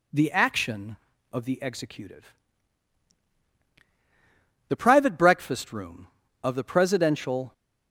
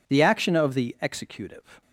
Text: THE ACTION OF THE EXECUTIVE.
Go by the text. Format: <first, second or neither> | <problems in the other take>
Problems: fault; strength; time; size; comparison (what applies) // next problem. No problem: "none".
second | goes on to say "The private breakfast room of the Presidential"; strong; from 4.6 s on; 2.8 s long